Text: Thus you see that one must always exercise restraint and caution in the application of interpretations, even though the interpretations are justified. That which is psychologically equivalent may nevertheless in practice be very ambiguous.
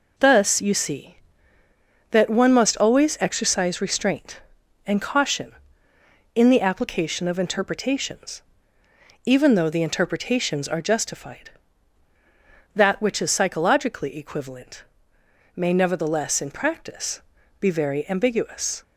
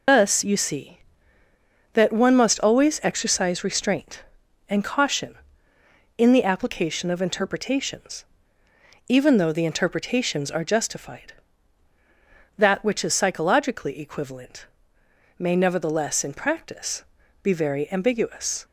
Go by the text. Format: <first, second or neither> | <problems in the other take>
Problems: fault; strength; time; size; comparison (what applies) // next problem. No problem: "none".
first | loses the start of "Thus"; at 0.0 s; 70 ms // pauses between "equivalent" and "may"; noticeable; at 14.6 s; 0.70 s long; noticeable in the first // pauses between "practice" and "be"; at 17.0 s; 0.40 s long; also in the first